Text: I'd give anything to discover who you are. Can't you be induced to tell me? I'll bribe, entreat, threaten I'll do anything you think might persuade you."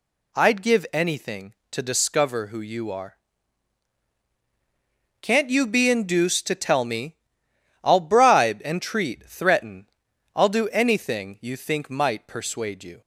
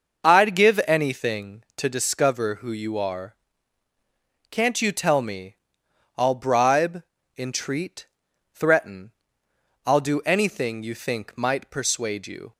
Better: first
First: pauses between "threaten" and "I'll"; noticeable; at 9.8 s; 0.46 s long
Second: starts louder than the rest; noticeable; until 1.2 s; 6 dB // skips "be induced to"; at 4.9 s // pauses between "threaten" and "I'll"; noticeable; at 9.1 s; 0.74 s long

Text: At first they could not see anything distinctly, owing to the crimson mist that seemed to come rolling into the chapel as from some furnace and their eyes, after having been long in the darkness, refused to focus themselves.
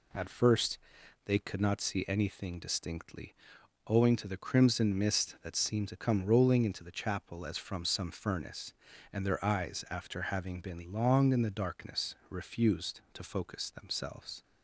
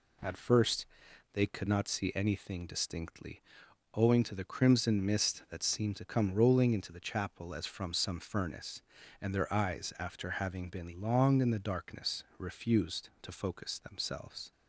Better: neither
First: pauses between "first" and "they"; noticeable; at 0.7 s; 0.48 s long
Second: pauses between "first" and "they"; noticeable; at 0.8 s; 0.48 s long

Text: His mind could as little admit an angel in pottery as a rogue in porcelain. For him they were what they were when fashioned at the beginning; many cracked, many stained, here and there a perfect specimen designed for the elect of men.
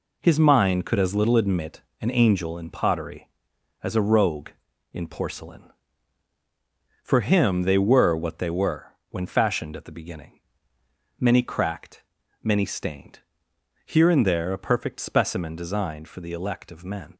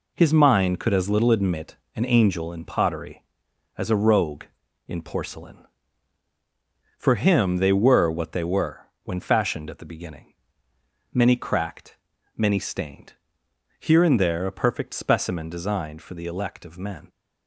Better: neither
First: pauses between "admit" and "an"; slight; at 1.8 s; 0.20 s long // pauses between "were" and "when"; slight; at 8.9 s; 0.16 s long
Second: pauses between "admit" and "an"; slight; at 1.7 s; 0.20 s long // pauses between "were" and "when"; slight; at 8.8 s; 0.16 s long

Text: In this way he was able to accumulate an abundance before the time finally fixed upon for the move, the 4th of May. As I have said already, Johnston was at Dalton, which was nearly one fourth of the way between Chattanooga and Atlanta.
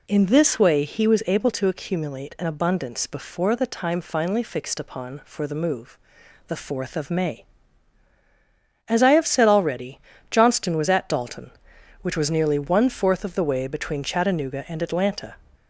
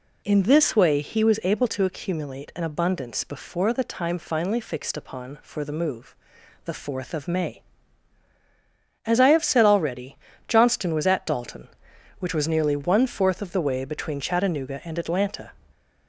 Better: neither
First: none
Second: none

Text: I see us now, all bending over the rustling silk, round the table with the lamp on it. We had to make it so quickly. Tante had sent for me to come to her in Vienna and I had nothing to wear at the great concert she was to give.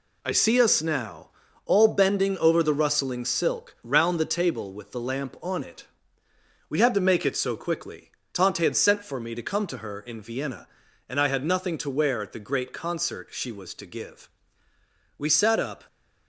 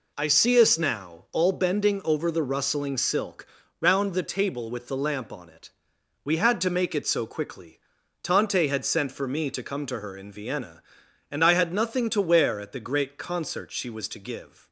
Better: second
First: goes on to say "We sat up"; noticeable; from 15.1 s on; 0.68 s long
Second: none

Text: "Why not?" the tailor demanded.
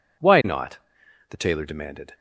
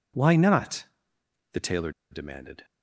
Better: first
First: none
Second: pauses between "tailor" and "demanded"; slight; at 1.9 s; 0.20 s long

